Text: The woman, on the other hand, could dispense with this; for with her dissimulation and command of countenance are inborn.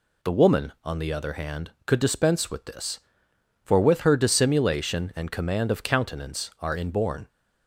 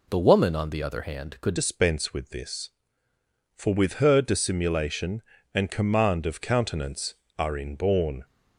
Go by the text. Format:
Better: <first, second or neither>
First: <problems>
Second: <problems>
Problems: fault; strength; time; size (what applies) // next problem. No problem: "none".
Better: first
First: none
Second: changes voice at "dispense"; from 1.5 s on; 6.7 s long